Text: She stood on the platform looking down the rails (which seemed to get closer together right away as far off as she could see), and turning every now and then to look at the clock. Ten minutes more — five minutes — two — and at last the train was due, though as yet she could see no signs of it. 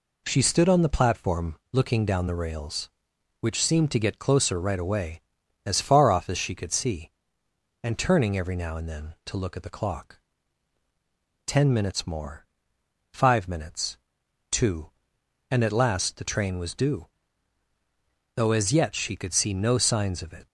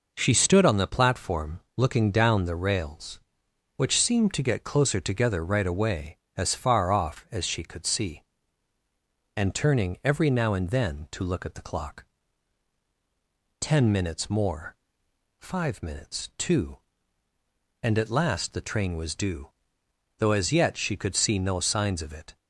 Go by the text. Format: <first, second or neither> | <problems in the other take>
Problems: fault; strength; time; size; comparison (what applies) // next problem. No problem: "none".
second | pauses between "platform" and "looking"; slight; at 1.5 s; 0.16 s long; slight in the second // skips "together"; at 4.5 s